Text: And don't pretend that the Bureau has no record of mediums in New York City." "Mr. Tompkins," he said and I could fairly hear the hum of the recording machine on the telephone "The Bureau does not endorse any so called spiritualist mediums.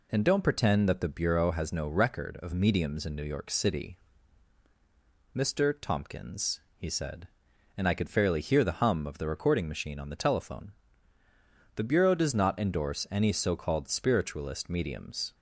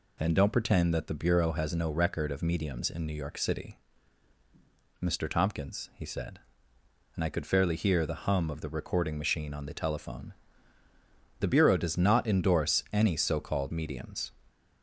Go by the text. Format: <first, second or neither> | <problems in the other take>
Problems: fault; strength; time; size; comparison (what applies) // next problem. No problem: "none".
first | pauses between "telephone" and "The"; at 10.3 s; 1.0 s long; also in the first // skips "spiritualist"; at 13.7 s